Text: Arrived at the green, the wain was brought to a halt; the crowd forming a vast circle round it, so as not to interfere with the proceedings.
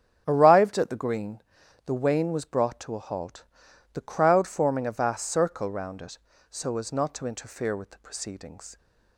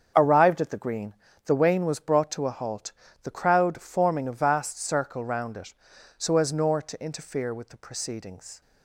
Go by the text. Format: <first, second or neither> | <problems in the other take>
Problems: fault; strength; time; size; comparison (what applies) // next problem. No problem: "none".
first | starts louder than the rest; strong; until 1.1 s; 7 dB; strong in the first // says "nor" for "not"; at 6.5 s